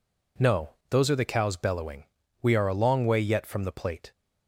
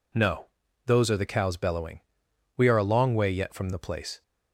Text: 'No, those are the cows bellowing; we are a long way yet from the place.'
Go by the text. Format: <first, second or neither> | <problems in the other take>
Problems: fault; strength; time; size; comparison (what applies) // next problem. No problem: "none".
second | says "plate" for "place"; at 3.7 s